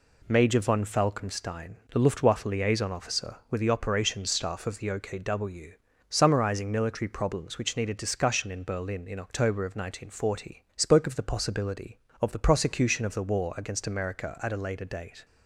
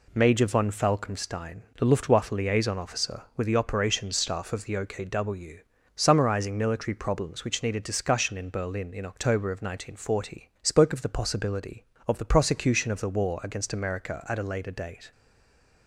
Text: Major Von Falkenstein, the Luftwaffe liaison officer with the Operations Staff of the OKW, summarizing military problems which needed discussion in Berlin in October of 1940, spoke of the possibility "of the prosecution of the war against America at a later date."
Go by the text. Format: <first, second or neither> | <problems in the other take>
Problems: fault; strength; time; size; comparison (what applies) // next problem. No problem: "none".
first | stays silent after the last word; slight; from 15.1 s on; 0.7 s long